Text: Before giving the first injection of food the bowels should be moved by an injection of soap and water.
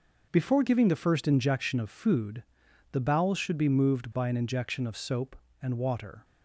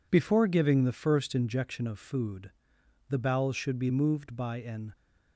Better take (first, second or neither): first